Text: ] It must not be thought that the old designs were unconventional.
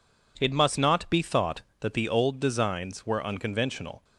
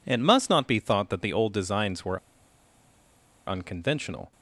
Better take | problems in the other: first | pauses between "were" and "unconventional"; strong; at 2.1 s; 1.2 s long

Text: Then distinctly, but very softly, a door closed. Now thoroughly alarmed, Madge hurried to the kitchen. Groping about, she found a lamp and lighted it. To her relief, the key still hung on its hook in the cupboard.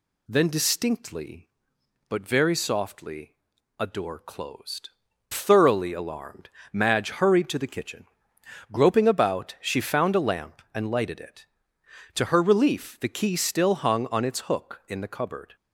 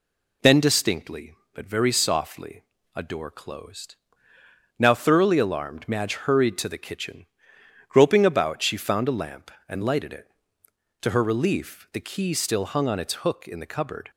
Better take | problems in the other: second | skips "Now"; at 5.0 s

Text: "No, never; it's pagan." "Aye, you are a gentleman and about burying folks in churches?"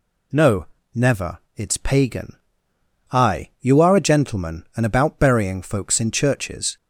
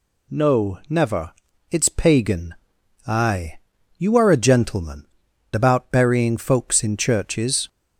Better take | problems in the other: first | skips "and"; at 5.2 s

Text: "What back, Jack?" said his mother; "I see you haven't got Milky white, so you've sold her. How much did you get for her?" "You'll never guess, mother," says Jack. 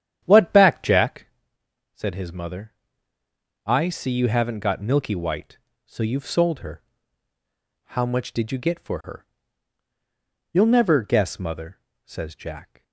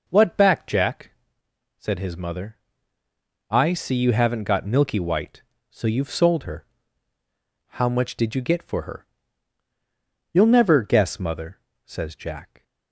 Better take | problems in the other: second | starts louder than the rest; strong; until 1.3 s; 10 dB

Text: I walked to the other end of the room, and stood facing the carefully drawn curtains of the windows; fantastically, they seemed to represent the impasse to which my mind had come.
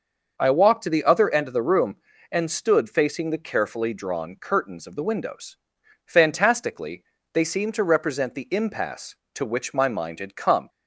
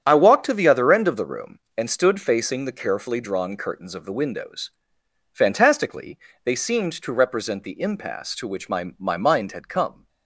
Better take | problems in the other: first | starts louder than the rest; strong; until 1.0 s; 9 dB; noticeable in the first // says "my" twice; at 8.9 s

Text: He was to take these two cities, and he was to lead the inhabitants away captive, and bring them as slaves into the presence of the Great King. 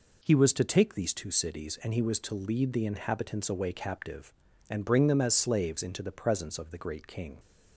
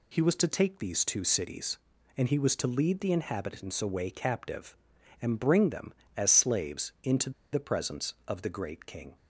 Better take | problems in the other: first | pauses between "into" and "the"; slight; at 7.3 s; 0.22 s long

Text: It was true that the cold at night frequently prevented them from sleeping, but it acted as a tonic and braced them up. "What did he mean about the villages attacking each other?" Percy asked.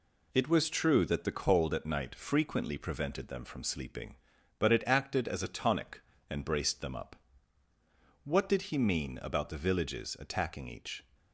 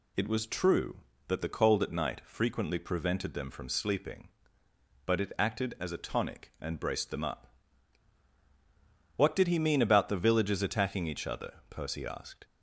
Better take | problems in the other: second | stops before "other Percy asked"; at 11.1 s

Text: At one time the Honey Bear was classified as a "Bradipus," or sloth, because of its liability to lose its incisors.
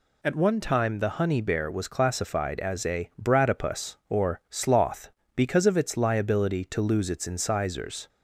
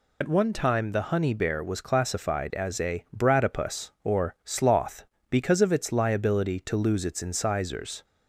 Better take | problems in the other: first | loses the start of "At"; at 0.2 s; 45 ms

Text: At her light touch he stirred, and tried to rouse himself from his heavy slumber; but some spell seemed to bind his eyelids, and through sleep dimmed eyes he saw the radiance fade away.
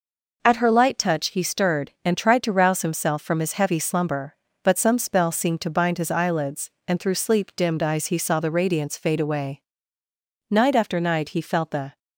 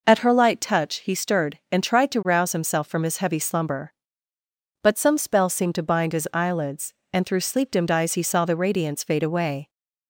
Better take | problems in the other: second | goes on to say "Night after night he felt the"; from 10.4 s on; 1.5 s long

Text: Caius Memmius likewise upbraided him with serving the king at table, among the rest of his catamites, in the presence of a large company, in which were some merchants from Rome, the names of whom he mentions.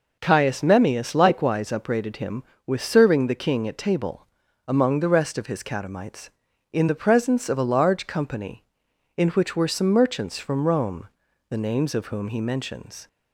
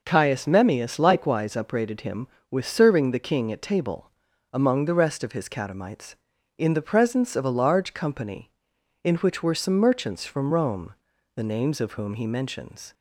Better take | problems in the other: neither | none

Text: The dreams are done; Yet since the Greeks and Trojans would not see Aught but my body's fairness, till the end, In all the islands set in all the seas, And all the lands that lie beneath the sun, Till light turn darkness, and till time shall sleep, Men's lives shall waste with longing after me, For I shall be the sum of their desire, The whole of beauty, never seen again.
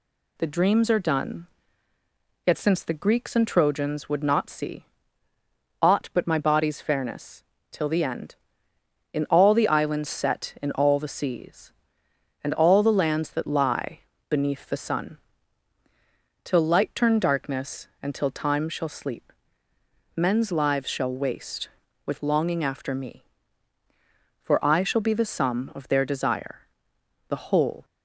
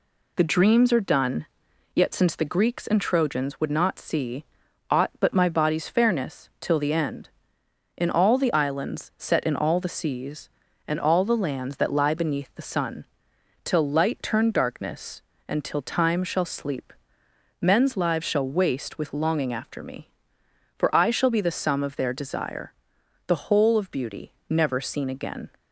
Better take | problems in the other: second | pauses between "see" and "Aught"; noticeable; at 4.8 s; 0.96 s long; noticeable in the second // pauses between "lie" and "beneath"; slight; at 14.0 s; 0.28 s long // stops before "of beauty never seen again"; at 27.8 s

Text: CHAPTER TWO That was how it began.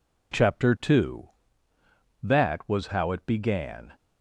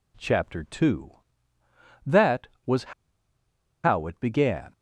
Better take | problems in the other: first | pauses between "was" and "how"; noticeable; at 2.9 s; 0.92 s long

